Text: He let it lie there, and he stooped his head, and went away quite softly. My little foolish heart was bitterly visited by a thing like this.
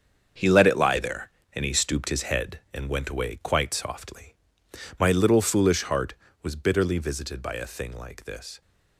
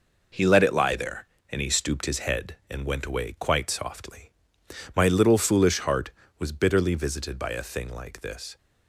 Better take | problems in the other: second | gets quieter; strong; throughout; 10 dB

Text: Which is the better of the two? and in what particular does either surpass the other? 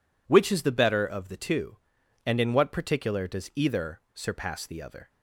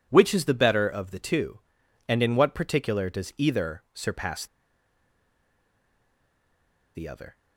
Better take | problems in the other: first | pauses between "surpass" and "the"; strong; at 4.4 s; 2.4 s long

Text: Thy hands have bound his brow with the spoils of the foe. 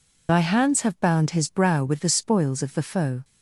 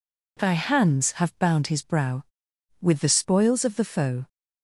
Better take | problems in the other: second | loses the start of "Thy"; at 0.2 s; 80 ms

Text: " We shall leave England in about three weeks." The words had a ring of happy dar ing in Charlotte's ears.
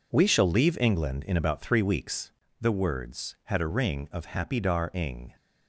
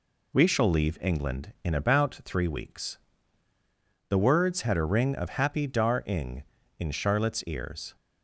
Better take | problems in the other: second | stops before "in Charlotte's ears"; at 5.3 s

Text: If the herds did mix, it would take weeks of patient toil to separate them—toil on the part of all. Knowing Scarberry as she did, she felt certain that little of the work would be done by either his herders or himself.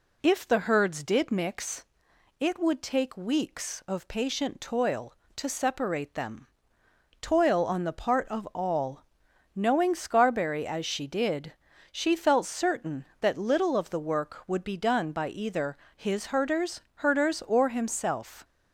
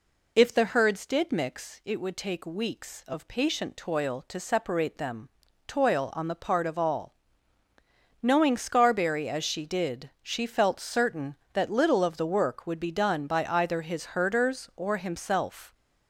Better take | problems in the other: second | pauses between "either" and "his"; slight; at 15.7 s; 0.20 s long // says "herders" twice; at 16.9 s

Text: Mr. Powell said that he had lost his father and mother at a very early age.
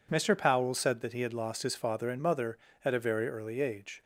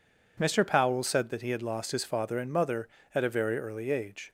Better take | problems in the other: neither | none

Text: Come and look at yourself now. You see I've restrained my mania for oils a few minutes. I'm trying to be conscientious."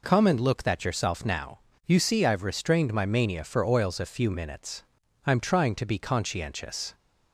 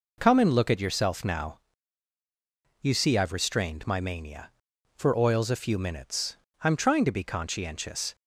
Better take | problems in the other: second | says "that" for "at"; at 0.6 s

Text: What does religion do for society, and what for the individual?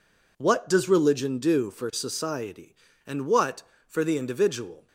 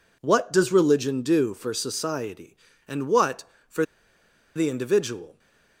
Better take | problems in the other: first | pauses between "for" and "the"; noticeable; at 3.8 s; 0.71 s long

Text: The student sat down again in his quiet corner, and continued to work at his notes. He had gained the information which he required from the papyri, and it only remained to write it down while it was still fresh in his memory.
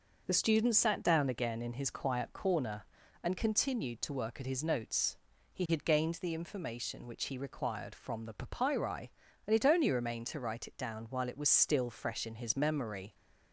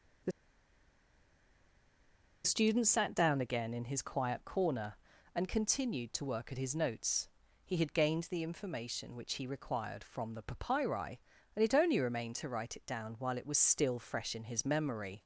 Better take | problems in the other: first | pauses between "The" and "student"; strong; at 0.3 s; 2.1 s long

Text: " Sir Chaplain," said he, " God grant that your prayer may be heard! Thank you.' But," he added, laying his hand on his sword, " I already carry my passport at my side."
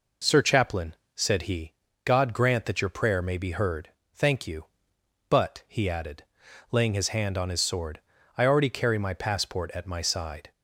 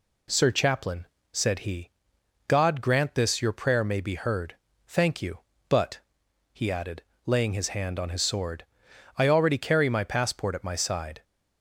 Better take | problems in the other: first | says "this" for "that"; at 3.1 s

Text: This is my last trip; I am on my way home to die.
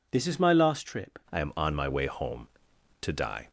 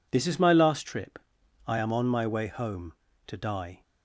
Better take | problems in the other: second | changes voice at "I"; from 1.2 s on; 2.2 s long

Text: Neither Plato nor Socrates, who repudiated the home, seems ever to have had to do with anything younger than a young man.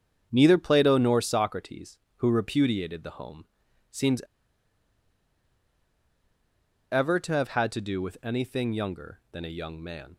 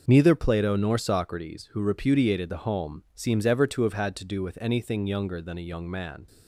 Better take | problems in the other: second | starts louder than the rest; strong; until 1.3 s; 7.5 dB // pauses between "seems" and "ever"; strong; at 4.2 s; 2.6 s long

